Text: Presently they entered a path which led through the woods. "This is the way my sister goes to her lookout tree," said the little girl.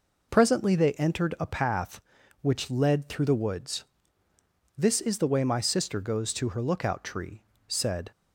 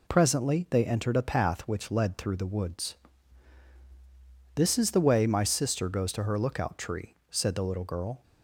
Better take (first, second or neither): second